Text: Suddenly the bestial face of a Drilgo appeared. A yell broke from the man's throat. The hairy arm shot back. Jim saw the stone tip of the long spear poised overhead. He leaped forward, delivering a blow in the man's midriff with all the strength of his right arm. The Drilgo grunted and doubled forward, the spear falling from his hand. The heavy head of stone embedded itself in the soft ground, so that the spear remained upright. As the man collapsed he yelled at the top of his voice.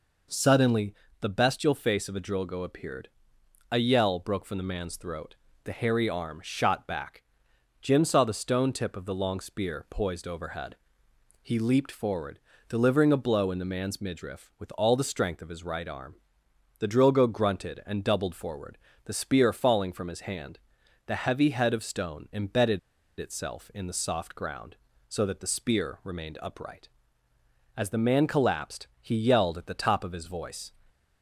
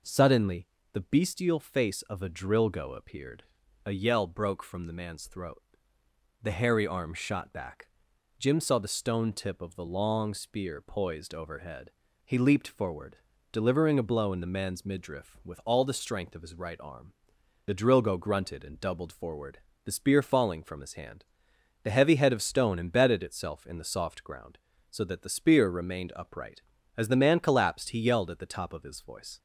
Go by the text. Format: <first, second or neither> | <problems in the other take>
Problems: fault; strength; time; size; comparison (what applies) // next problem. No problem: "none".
second | pauses between "Suddenly" and "the"; slight; at 0.9 s; 0.28 s long; slight in the second // pauses between "embedded" and "itself"; at 22.7 s; 0.41 s long